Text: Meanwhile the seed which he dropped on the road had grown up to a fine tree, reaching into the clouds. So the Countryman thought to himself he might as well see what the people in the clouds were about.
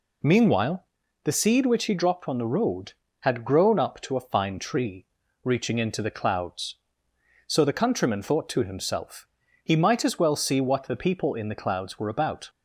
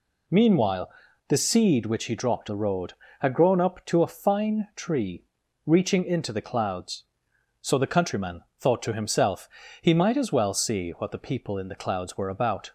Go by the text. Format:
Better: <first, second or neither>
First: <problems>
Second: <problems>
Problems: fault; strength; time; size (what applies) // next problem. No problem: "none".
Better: first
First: pauses between "Meanwhile" and "the"; at 0.8 s; 0.38 s long // pauses between "himself" and "he"; slight; at 9.2 s; 0.36 s long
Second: pauses between "Meanwhile" and "the"; at 0.9 s; 0.38 s long // skips "on"; at 2.4 s // pauses between "Countryman" and "thought"; slight; at 8.4 s; 0.18 s long // pauses between "himself" and "he"; slight; at 9.4 s; 0.32 s long